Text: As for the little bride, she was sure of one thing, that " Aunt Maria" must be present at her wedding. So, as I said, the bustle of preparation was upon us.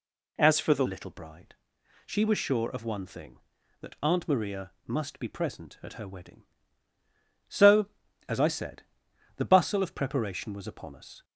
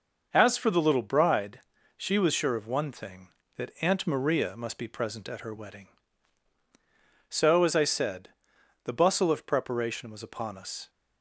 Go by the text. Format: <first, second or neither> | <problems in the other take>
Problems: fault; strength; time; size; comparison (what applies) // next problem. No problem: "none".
second | changes voice at "little"; from 0.8 s on; 10.4 s long